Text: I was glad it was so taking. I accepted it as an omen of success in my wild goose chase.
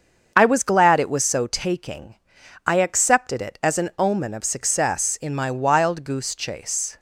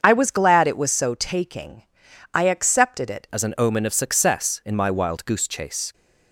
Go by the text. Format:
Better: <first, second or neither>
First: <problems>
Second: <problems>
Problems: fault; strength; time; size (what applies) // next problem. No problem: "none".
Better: first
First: starts louder than the rest; until 1.3 s; 6.5 dB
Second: starts louder than the rest; until 1.0 s; 7 dB // changes voice at "as"; from 3.3 s on; 2.6 s long